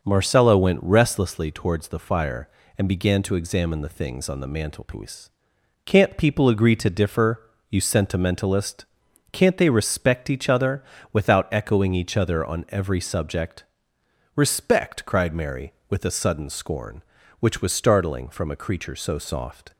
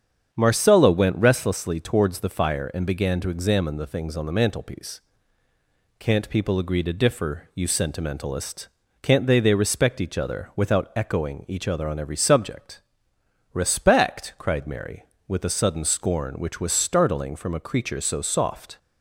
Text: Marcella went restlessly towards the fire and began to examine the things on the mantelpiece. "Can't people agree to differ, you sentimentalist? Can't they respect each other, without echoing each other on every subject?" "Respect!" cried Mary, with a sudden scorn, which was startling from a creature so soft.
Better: first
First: none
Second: starts louder than the rest; strong; until 1.3 s; 8 dB // says "they" twice; at 9.3 s

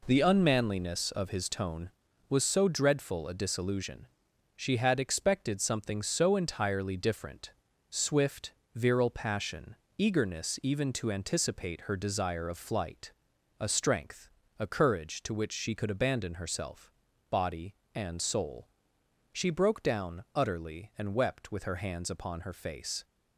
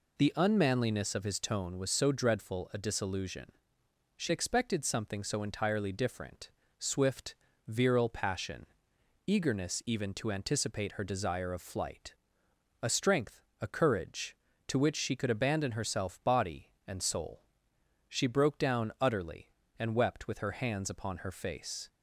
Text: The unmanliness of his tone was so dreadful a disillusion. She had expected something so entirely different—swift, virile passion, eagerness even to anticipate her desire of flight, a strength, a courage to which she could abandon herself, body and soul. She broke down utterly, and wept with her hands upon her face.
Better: first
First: none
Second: skips "had"; at 4.2 s

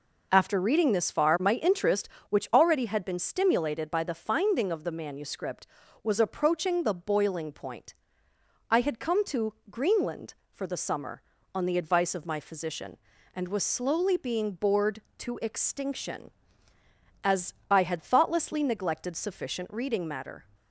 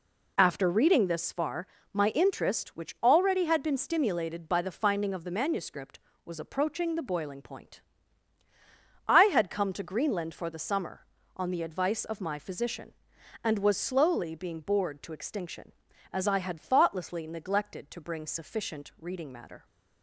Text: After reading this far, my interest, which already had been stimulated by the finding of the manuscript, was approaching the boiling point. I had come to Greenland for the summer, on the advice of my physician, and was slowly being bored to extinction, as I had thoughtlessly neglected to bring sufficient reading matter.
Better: second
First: pauses between "to" and "Greenland"; slight; at 9.5 s; 0.16 s long // pauses between "as" and "I"; slight; at 17.5 s; 0.16 s long // skips "to bring"; at 19.1 s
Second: none

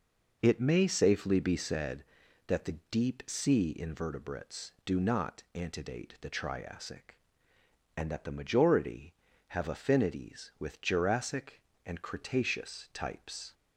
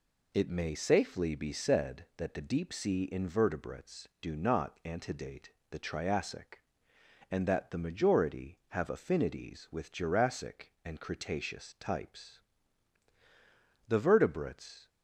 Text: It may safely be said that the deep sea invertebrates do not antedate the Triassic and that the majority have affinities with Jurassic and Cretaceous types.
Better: first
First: none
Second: pauses between "antedate" and "the"; slight; at 5.5 s; 0.20 s long // goes on to say "The vertebrates"; noticeable; from 13.8 s on; 1.0 s long

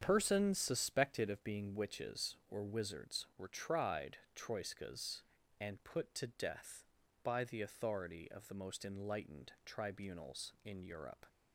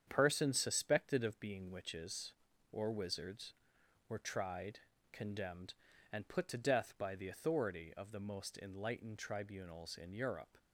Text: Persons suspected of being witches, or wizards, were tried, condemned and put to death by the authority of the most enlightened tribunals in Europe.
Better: second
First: starts louder than the rest; strong; until 1.0 s; 8 dB // says "troiskas" for "condemned"; at 4.3 s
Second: starts louder than the rest; strong; until 1.0 s; 8 dB

